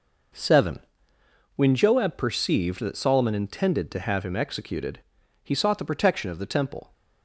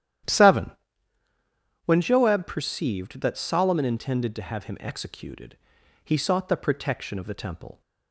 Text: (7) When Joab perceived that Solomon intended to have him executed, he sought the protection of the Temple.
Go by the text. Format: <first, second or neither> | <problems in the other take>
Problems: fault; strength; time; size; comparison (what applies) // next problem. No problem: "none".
first | starts louder than the rest; strong; until 2.0 s; 11.5 dB